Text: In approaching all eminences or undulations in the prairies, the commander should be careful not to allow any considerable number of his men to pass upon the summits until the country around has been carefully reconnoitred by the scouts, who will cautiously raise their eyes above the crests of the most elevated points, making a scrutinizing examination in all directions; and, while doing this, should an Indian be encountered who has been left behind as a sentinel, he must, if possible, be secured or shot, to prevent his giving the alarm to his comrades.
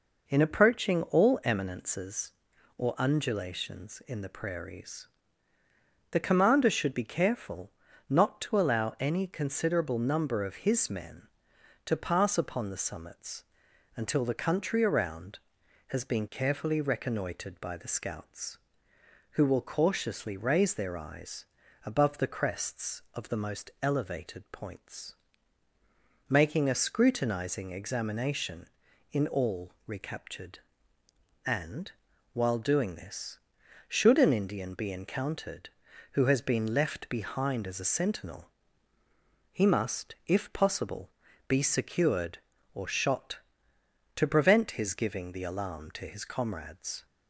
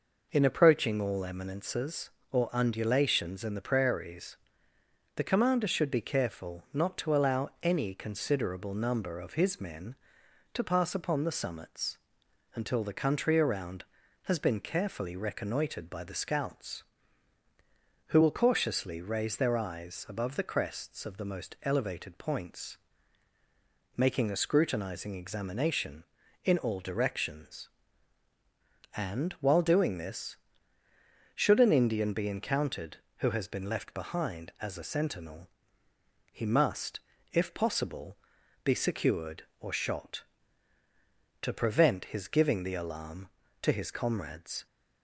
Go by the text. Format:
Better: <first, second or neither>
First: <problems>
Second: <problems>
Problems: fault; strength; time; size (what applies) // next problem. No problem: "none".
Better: second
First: pauses between "careful" and "not"; at 7.6 s; 0.40 s long // pauses between "summits" and "until"; noticeable; at 13.4 s; 0.52 s long // pauses between "eyes" and "above"; at 21.4 s; 0.42 s long // says "recaptured" for "directions"; at 29.8 s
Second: pauses between "summits" and "until"; noticeable; at 11.9 s; 0.58 s long